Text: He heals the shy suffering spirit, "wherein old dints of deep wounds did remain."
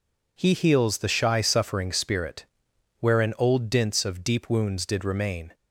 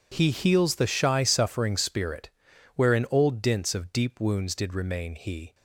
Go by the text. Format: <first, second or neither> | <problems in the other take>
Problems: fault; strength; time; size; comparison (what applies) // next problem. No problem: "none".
first | goes on to say "He"; slight; from 5.1 s on; 0.40 s long